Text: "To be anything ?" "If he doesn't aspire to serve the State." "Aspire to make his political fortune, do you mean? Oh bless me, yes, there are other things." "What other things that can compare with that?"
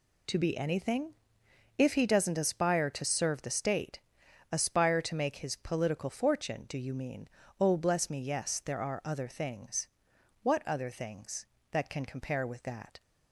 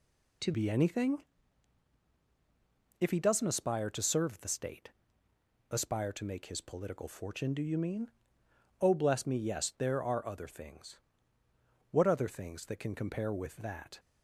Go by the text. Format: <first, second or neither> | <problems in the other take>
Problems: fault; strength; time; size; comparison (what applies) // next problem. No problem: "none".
first | changes voice at "be"; from 0.5 s on; 13.4 s long